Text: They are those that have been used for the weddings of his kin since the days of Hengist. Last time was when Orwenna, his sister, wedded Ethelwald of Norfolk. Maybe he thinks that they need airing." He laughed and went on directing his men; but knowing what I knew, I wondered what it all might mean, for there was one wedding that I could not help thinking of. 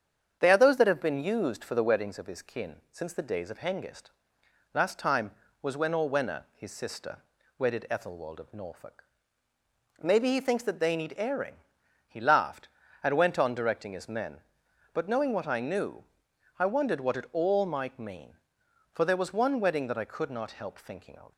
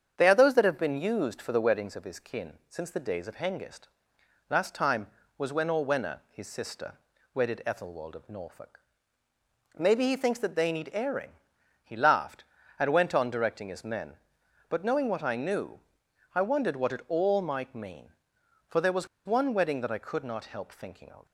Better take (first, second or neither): first